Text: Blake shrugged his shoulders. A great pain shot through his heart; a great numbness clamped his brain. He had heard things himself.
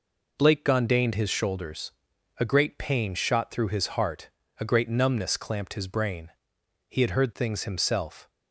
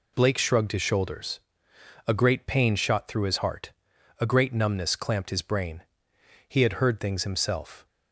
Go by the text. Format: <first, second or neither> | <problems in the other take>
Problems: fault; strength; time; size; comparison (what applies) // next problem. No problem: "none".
second | says "gondained" for "shrugged"; at 0.6 s